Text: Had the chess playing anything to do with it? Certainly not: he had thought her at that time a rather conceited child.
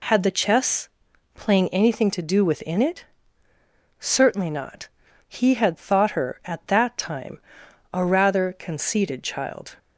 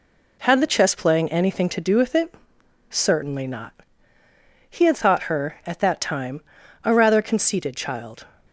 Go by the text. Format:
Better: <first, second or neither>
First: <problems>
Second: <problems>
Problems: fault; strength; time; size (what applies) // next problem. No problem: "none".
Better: second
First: pauses between "chess" and "playing"; at 0.8 s; 0.44 s long // says "within" for "with"; at 2.4 s // pauses between "time" and "a"; noticeable; at 7.3 s; 0.54 s long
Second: pauses between "time" and "a"; at 6.4 s; 0.42 s long